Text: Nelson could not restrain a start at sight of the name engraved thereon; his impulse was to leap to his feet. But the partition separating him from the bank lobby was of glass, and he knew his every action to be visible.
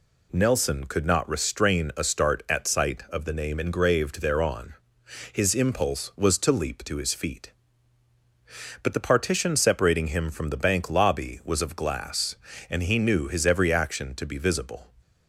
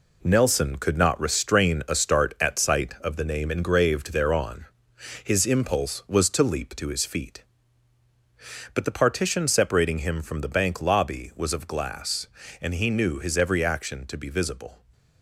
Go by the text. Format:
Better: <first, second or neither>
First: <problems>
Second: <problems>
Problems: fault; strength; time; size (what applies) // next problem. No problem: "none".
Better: first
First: none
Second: gets quieter; strong; throughout; 7.5 dB